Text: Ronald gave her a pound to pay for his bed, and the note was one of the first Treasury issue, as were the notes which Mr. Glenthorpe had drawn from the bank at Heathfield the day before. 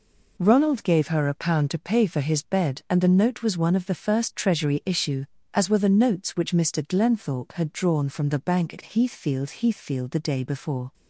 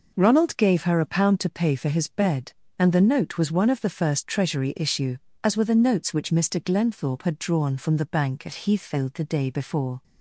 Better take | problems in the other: second | says "Heathfield" twice; at 9.5 s

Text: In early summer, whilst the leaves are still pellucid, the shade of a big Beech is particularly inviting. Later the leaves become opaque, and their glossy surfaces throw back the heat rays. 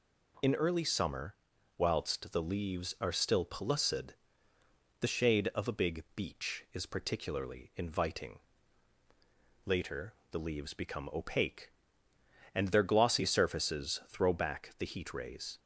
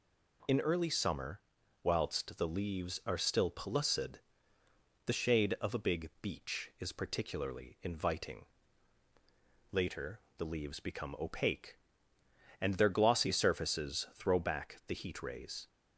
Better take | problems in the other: neither | pauses between "Later" and "the"; slight; the same in both

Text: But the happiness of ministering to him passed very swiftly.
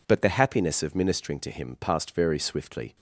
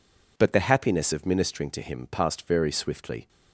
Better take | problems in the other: neither | none

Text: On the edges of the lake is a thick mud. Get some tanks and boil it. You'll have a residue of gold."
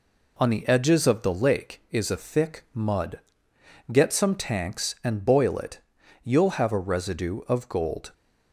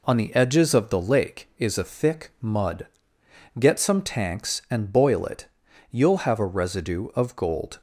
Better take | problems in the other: neither | none

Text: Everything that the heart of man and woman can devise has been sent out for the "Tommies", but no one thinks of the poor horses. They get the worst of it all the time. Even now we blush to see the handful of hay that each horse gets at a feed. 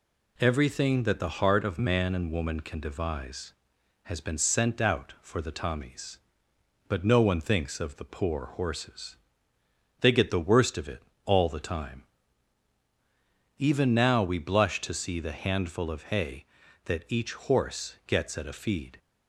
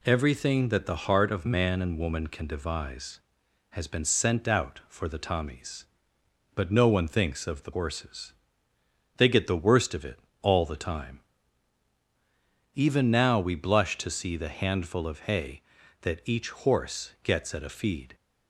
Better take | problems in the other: first | skips "poor"; at 7.7 s // pauses between "it" and "all"; slight; at 10.2 s; 0.20 s long; slight in the first

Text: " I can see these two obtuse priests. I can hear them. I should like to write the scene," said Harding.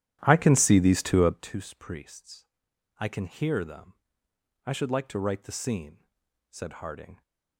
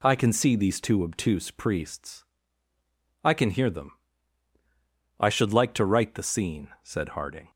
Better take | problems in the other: second | starts louder than the rest; strong; until 1.5 s; 11.5 dB

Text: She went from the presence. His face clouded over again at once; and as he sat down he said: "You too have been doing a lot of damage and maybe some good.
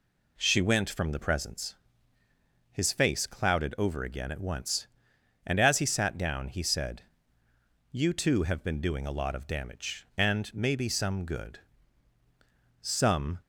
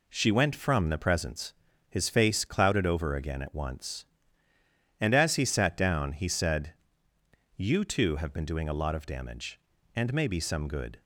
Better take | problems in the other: second | goes on to say "Some"; from 12.8 s on; 0.56 s long

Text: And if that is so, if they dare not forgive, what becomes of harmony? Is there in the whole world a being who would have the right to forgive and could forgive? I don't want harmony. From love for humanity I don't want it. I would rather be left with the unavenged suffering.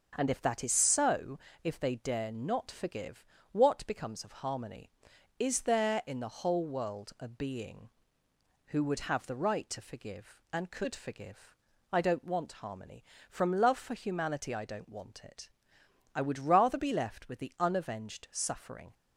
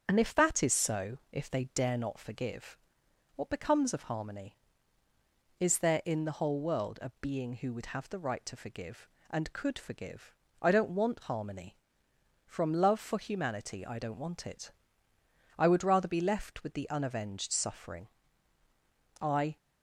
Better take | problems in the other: first | starts louder than the rest; strong; until 1.1 s; 7.5 dB; also in the first // goes on to say "I"; slight; from 19.2 s on; 0.36 s long

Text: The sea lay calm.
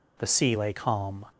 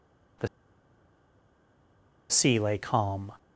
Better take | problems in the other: first | pauses between "The" and "sea"; strong; at 0.4 s; 1.8 s long

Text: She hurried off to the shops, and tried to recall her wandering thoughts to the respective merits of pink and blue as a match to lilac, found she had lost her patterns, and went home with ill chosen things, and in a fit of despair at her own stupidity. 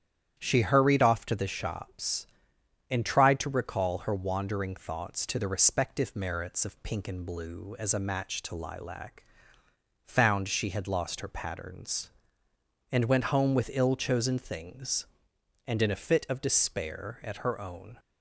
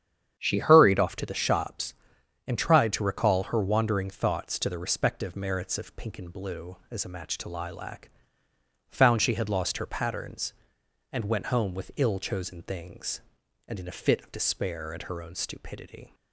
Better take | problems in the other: second | starts louder than the rest; strong; until 1.3 s; 9.5 dB; strong in the second // stops before "stupidity"; at 17.9 s

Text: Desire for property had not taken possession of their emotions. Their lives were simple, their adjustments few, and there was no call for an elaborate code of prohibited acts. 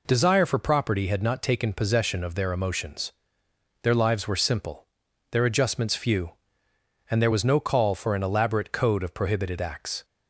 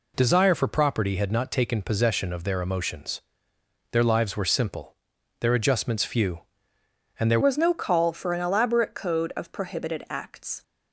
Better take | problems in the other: first | changes voice at "was"; from 7.4 s on; 3.2 s long

